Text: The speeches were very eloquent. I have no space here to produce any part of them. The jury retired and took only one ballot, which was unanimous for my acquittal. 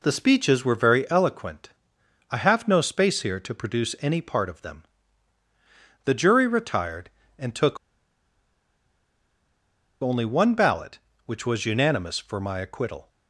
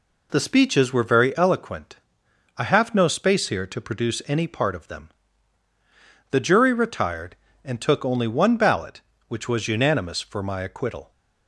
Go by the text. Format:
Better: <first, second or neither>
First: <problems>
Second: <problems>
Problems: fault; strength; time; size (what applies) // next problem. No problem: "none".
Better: second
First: pauses between "took" and "only"; strong; at 7.7 s; 2.2 s long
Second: none